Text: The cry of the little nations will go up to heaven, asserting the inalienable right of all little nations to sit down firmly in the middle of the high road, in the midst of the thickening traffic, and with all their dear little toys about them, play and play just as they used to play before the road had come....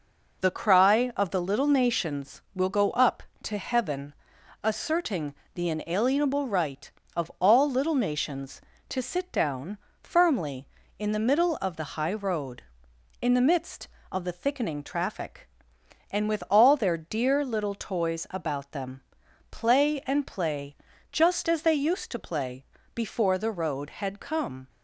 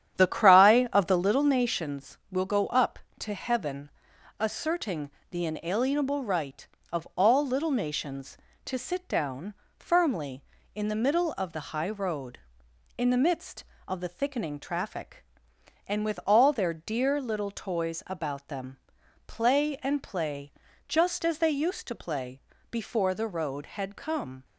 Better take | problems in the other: first | starts louder than the rest; strong; until 1.5 s; 10 dB // pauses between "asserting" and "the"; slight; at 5.1 s; 0.20 s long; slight in the first // pauses between "down" and "firmly"; slight; at 9.5 s; 0.22 s long; slight in the first // pauses between "play" and "just"; slight; at 20.5 s; 0.34 s long; slight in the first // pauses between "play" and "before"; slight; at 22.3 s; 0.32 s long; slight in the first

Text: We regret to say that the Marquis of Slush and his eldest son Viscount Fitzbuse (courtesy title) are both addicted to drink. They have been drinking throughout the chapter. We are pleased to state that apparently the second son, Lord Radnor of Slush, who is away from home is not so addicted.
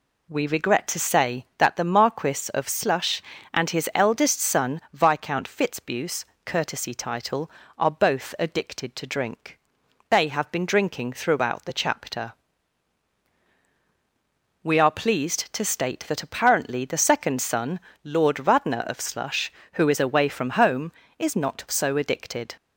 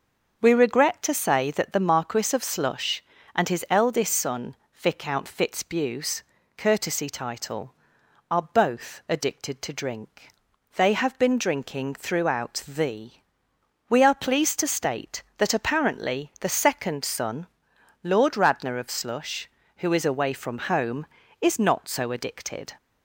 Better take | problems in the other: first | starts louder than the rest; until 1.4 s; 6 dB // pauses between "son" and "Viscount"; slight; at 4.5 s; 0.18 s long // skips "chapter"; at 13.4 s

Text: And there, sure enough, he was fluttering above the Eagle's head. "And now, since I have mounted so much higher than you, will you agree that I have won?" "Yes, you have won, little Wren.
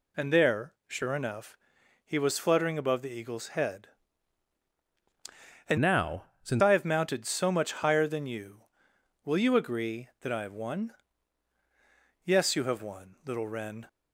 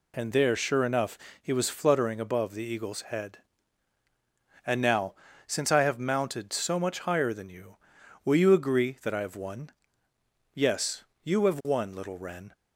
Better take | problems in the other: second | changes voice from "now" to "since"; from 5.7 to 6.6 s; 0.9 s long

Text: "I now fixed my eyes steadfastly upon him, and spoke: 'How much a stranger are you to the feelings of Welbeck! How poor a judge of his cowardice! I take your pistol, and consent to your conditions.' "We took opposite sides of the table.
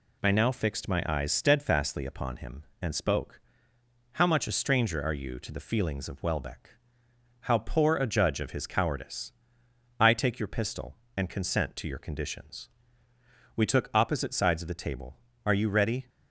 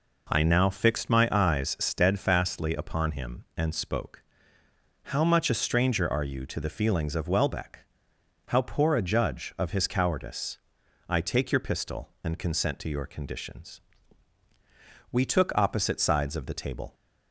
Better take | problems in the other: second | goes on to say "Are you ready"; noticeable; from 15.4 s on; 0.64 s long

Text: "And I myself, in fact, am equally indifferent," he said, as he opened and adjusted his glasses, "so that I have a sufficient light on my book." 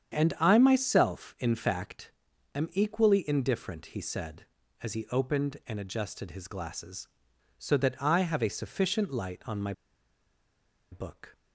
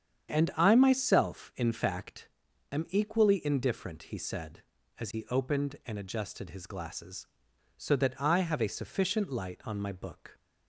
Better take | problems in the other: second | starts louder than the rest; strong; until 1.1 s; 8 dB; strong in the second // pauses between "my" and "book"; at 9.7 s; 1.1 s long

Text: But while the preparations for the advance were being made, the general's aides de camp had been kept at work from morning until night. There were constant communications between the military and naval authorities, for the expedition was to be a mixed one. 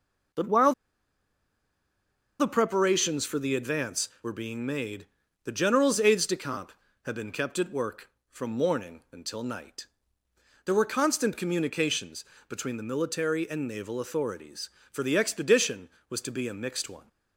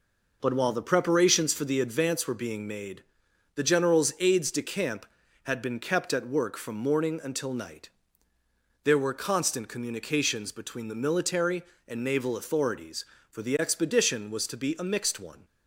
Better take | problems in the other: second | pauses between "while" and "the"; strong; at 0.7 s; 1.6 s long // pauses between "communications" and "between"; slight; at 12.2 s; 0.24 s long

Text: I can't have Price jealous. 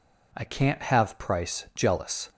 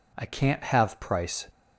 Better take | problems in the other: first | stops before "jealous"; at 1.4 s

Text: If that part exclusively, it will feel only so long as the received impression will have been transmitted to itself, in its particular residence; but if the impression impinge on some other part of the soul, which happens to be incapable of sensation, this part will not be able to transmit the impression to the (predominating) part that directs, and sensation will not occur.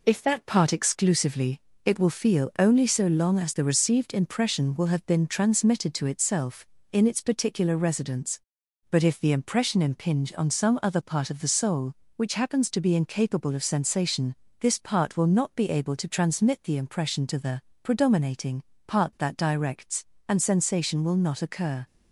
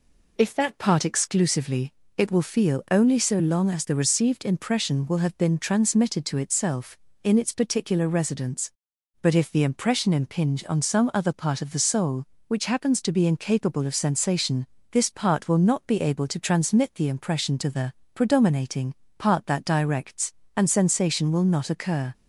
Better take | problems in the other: second | gets quieter; noticeable; throughout; 4 dB

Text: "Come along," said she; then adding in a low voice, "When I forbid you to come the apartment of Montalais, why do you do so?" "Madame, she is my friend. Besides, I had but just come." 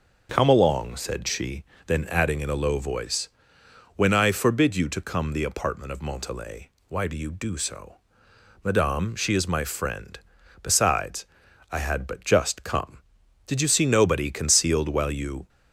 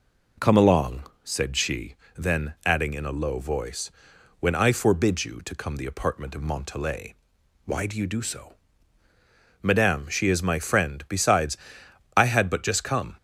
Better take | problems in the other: second | goes on to say "Did you see nobody concealed while you"; strong; from 13.4 s on; 2.0 s long

